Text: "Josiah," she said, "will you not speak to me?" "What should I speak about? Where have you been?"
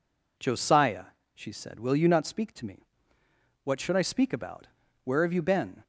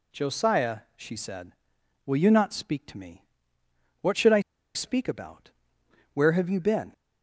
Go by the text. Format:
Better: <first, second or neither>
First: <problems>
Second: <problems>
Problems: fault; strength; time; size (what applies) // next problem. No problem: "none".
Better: first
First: none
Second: pauses between "I" and "speak"; slight; at 4.4 s; 0.33 s long